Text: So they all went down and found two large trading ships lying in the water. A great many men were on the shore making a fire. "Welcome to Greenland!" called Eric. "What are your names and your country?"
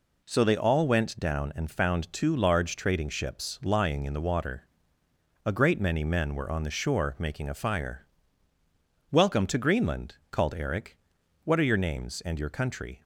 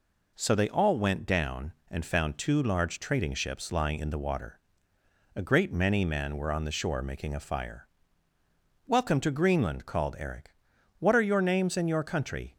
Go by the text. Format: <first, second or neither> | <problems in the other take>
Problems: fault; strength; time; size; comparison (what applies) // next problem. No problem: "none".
neither | none